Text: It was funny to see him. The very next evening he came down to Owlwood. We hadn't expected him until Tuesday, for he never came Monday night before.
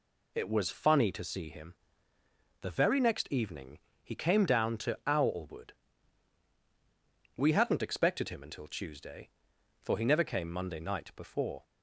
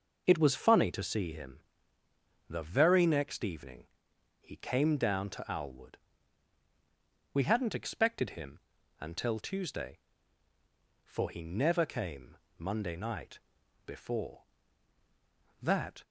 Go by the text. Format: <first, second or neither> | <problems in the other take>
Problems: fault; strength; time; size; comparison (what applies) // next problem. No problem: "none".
first | pauses between "evening" and "he"; noticeable; at 3.8 s; 0.54 s long; slight in the first // pauses between "him" and "until"; at 8.5 s; 0.40 s long // pauses between "came" and "Monday"; slight; at 12.3 s; 0.18 s long // pauses between "night" and "before"; noticeable; at 13.3 s; 0.46 s long // goes on to say "That"; slight; from 15.5 s on; 0.44 s long